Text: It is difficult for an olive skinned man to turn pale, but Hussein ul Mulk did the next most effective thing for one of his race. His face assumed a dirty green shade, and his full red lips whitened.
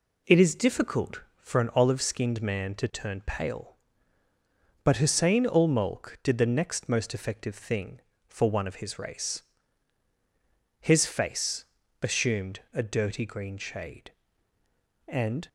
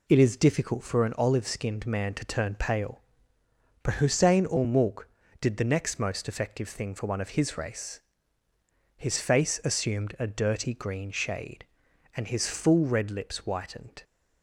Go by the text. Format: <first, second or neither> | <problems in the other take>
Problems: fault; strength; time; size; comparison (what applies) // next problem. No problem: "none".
second | pauses between "face" and "assumed"; at 11.6 s; 0.38 s long // stops before "his full red lips whitened"; at 15.4 s